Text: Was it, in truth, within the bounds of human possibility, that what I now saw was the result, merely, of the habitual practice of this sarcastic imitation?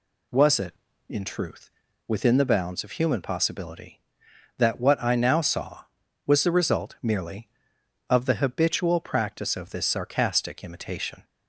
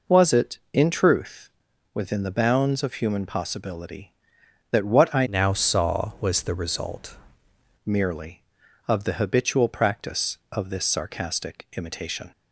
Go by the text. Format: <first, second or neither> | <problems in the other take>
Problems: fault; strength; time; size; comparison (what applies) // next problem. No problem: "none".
first | changes voice from "now" to "result"; from 5.2 to 7.1 s; 1.9 s long